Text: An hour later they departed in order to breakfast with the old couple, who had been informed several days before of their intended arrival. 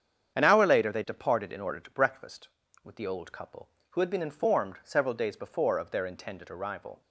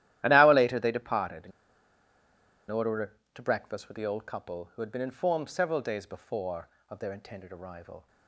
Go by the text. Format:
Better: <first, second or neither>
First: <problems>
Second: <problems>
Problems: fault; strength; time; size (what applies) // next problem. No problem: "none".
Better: first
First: starts louder than the rest; strong; until 1.4 s; 8 dB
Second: starts louder than the rest; strong; until 1.2 s; 13 dB // pauses between "in" and "order"; at 1.5 s; 1.1 s long